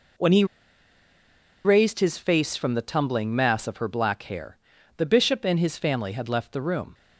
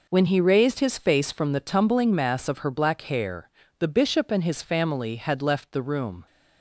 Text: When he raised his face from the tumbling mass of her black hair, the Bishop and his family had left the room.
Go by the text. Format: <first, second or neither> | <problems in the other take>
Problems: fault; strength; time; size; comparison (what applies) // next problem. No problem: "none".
second | pauses between "he" and "raised"; at 0.4 s; 1.2 s long